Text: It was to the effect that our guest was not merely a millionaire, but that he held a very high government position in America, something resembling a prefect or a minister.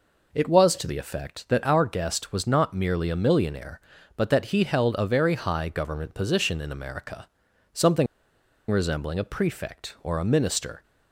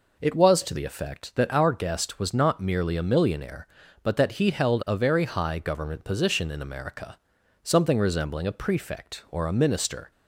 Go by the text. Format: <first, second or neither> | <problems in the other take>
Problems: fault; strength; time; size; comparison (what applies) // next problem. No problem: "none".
second | pauses between "something" and "resembling"; noticeable; at 8.0 s; 0.64 s long